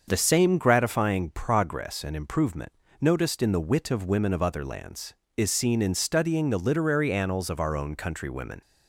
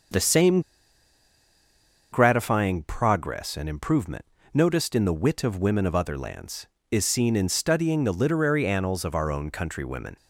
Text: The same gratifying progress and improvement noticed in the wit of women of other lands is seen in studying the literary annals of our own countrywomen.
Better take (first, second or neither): first